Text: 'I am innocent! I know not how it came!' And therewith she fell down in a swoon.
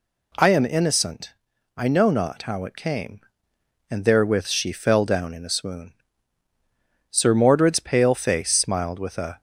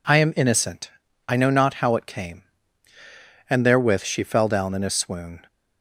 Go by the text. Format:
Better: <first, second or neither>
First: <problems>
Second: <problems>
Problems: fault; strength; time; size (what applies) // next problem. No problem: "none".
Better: second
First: goes on to say "Sir Mordred's pale face smiled with a"; strong; from 7.1 s on; 2.3 s long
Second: none